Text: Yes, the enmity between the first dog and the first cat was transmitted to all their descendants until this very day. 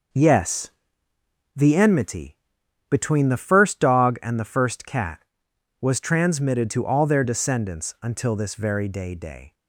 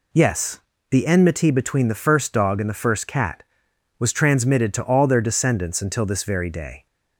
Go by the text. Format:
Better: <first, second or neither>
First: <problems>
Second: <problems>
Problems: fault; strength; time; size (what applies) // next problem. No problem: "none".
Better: second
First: pauses between "enmity" and "between"; noticeable; at 2.3 s; 0.52 s long // says "day" twice; at 9.1 s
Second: none